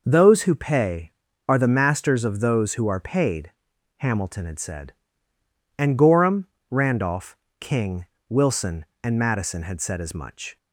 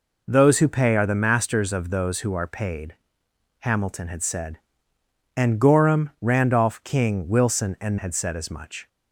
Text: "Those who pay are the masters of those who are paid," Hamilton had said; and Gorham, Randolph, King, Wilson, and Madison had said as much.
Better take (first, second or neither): first